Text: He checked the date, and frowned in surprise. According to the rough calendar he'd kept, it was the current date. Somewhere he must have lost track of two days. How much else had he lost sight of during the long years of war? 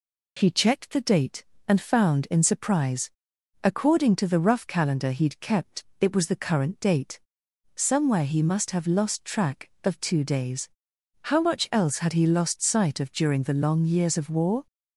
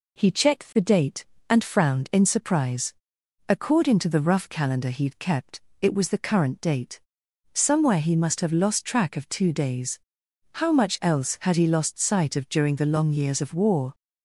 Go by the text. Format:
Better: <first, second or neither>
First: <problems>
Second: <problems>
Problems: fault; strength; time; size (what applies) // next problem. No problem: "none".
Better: second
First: says "found" for "frowned"; at 1.8 s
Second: none